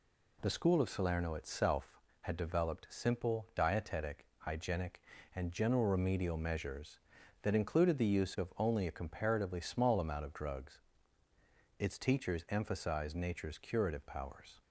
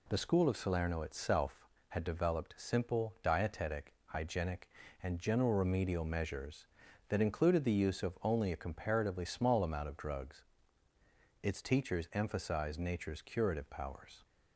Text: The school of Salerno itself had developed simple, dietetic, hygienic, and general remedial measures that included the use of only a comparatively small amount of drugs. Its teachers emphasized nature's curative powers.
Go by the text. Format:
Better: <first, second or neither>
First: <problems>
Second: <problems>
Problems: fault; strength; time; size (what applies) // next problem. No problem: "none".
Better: neither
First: none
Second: none